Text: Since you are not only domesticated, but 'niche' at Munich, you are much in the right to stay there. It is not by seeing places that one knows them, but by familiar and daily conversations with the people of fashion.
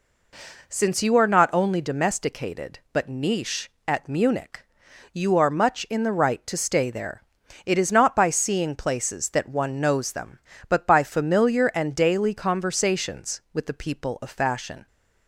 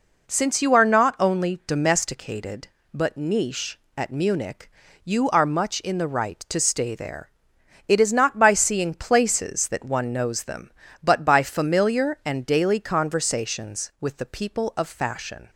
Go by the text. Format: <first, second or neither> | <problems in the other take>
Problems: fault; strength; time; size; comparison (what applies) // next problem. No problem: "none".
neither | none